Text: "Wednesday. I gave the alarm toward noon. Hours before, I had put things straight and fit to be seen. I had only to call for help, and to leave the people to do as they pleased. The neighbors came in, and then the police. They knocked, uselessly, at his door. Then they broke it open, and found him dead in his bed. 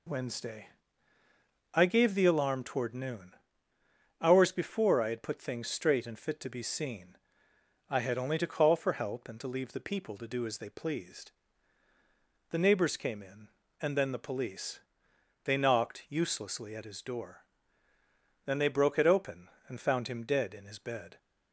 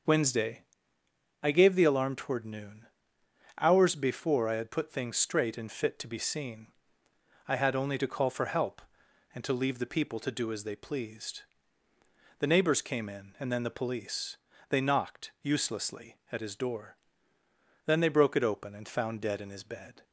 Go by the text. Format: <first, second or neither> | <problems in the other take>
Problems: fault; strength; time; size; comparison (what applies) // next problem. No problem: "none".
first | starts louder than the rest; until 1.8 s; 7 dB // skips "him"; at 19.2 s